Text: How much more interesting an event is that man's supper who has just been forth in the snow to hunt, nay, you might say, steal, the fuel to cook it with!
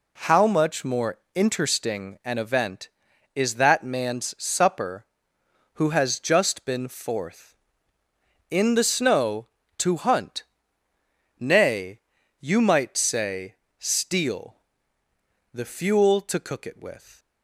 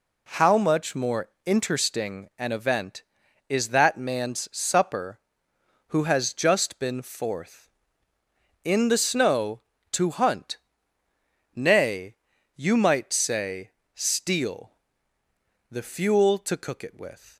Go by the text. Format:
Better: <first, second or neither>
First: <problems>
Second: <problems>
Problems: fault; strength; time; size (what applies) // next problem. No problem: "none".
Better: neither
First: pauses between "more" and "interesting"; slight; at 1.1 s; 0.18 s long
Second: pauses between "more" and "interesting"; slight; at 1.2 s; 0.18 s long